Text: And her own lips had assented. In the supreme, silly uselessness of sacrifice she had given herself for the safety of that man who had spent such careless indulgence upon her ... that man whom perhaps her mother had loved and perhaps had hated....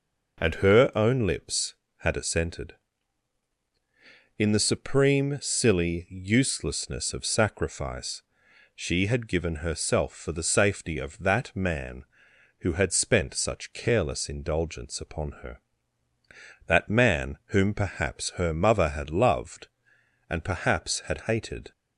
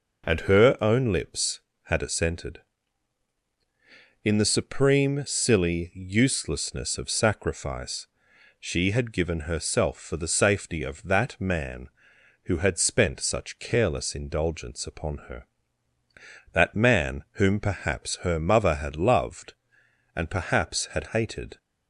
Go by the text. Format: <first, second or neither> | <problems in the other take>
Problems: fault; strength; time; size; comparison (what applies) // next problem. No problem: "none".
neither | pauses between "sacrifice" and "she"; noticeable; the same in both